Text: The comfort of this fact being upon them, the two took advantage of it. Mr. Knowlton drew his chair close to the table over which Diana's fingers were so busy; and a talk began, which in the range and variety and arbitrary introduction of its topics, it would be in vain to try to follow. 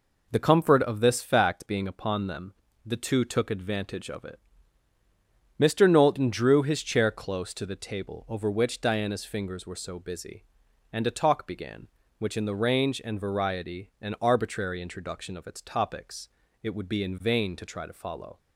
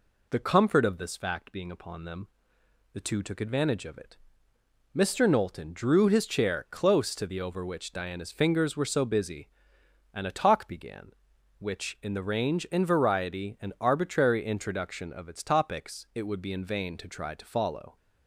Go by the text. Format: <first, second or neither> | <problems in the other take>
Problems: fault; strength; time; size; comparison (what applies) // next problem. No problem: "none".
first | skips "table"; at 7.4 s